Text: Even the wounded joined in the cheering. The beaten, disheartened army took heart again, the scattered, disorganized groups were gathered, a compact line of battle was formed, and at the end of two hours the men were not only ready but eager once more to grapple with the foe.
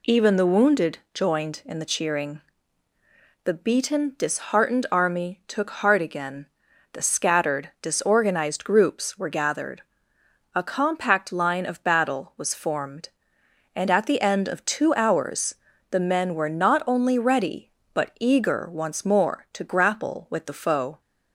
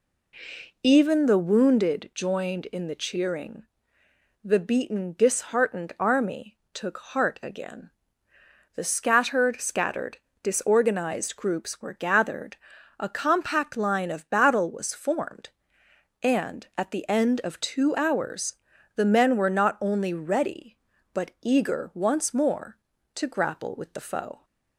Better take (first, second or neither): first